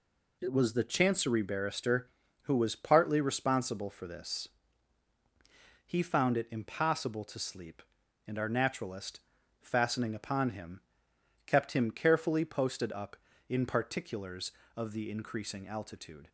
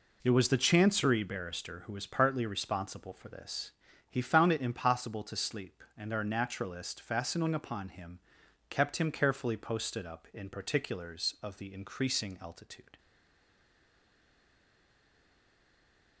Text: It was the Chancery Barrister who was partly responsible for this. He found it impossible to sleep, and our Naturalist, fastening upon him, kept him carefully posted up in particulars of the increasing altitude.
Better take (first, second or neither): first